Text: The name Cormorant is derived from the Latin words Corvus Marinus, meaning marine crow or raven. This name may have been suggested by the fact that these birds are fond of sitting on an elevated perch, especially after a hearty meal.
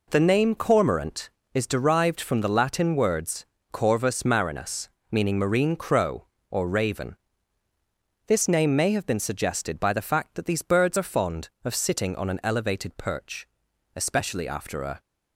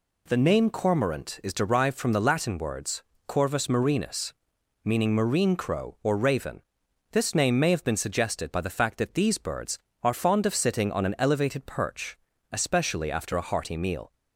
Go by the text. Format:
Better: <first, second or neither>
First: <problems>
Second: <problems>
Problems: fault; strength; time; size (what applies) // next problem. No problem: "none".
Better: second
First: pauses between "words" and "Corvus"; slight; at 3.4 s; 0.28 s long // stops before "hearty meal"; at 14.9 s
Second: pauses between "words" and "Corvus"; slight; at 3.0 s; 0.28 s long